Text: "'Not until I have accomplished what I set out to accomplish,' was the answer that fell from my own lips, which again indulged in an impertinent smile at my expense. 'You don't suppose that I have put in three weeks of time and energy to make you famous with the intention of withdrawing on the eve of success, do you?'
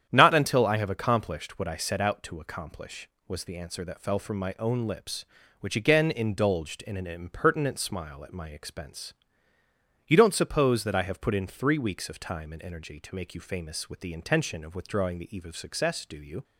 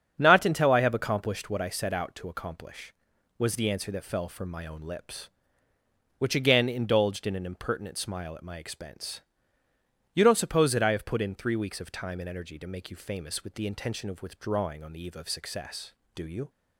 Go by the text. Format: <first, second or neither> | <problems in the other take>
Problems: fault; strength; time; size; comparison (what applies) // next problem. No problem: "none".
second | starts louder than the rest; strong; until 1.1 s; 9.5 dB; strong in the second // skips "on"; at 15.1 s